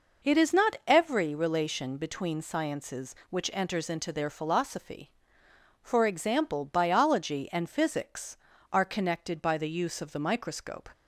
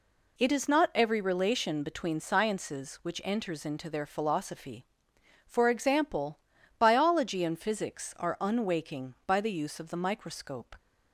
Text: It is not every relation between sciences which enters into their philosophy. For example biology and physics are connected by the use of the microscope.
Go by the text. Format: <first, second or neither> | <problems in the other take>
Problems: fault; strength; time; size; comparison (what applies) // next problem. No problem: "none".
first | pauses between "example" and "biology"; at 6.3 s; 0.40 s long // says "unwaking" for "connected"; at 8.3 s